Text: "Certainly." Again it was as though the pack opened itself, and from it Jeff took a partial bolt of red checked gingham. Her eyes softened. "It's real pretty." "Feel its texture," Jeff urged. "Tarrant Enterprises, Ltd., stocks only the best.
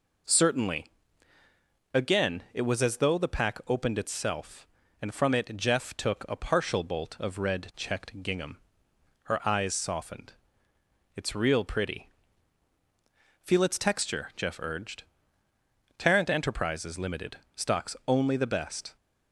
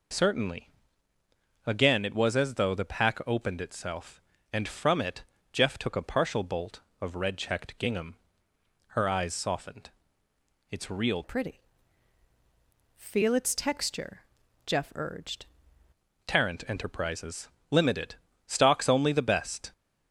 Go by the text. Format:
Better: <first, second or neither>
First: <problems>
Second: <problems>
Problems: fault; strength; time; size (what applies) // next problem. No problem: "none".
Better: first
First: none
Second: pauses between "it" and "Jeff"; slight; at 5.2 s; 0.30 s long // changes voice from "pretty" to "urged"; from 11.2 to 15.4 s; 4.2 s long